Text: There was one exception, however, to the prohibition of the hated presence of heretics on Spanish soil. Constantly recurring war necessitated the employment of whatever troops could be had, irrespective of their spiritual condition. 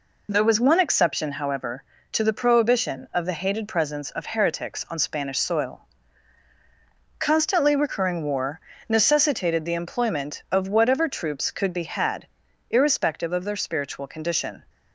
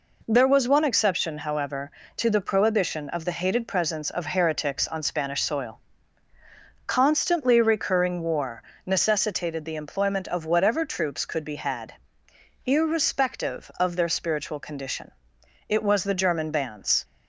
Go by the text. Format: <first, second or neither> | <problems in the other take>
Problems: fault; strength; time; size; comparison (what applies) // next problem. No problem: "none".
first | pauses between "war" and "necessitated"; slight; at 8.6 s; 0.24 s long; slight in the first // goes on to say "It was the German bands"; from 15.6 s on; 1.3 s long